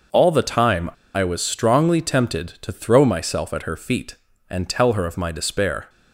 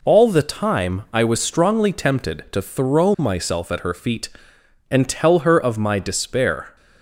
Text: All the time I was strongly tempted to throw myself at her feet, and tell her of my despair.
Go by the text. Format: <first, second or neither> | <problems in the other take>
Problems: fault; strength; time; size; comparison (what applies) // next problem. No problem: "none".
second | pauses between "time" and "I"; slight; at 0.8 s; 0.25 s long